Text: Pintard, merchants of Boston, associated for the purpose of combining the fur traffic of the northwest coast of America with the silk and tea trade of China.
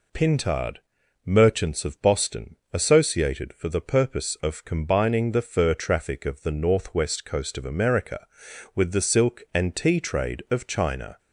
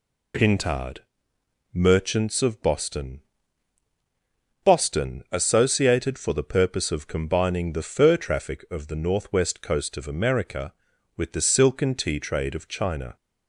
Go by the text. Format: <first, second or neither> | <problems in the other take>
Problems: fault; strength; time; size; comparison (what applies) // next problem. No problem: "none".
first | says "Boston" twice; at 4.6 s